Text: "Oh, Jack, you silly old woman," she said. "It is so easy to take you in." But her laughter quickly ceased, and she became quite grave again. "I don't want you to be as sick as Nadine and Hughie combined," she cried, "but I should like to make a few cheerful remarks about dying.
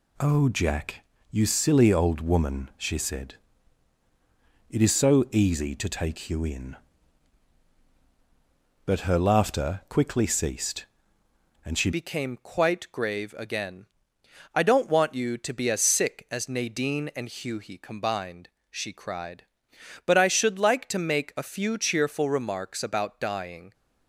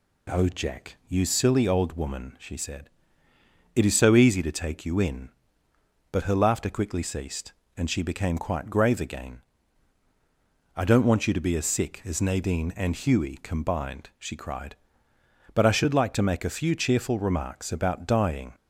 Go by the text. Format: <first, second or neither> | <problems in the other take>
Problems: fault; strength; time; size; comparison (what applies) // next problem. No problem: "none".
second | changes voice at "became"; from 11.9 s on; 11.8 s long